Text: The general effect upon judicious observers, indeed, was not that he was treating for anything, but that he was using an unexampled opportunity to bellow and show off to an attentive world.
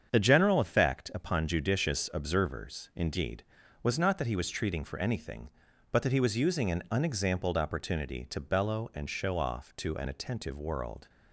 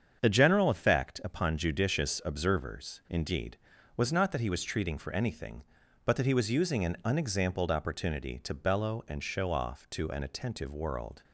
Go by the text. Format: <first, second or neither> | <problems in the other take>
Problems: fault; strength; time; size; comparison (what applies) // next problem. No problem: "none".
neither | starts louder than the rest; strong; the same in both